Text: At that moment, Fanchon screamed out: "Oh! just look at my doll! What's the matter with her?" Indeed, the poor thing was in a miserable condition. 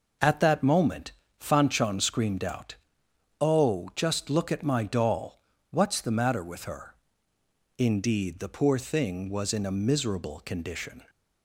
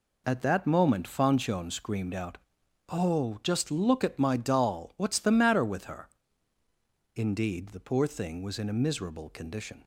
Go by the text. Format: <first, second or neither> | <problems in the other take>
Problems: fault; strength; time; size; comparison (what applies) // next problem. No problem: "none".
neither | none